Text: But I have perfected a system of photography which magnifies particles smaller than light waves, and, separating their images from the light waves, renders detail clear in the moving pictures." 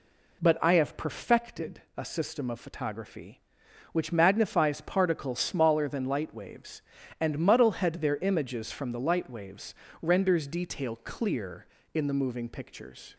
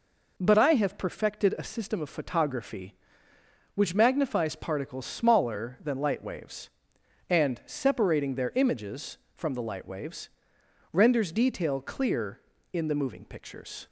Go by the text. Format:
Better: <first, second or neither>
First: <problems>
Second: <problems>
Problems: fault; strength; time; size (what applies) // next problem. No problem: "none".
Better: second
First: pauses between "perfected" and "a"; slight; at 1.8 s; 0.16 s long // says "muddlehead" for "separating"; at 7.3 s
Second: none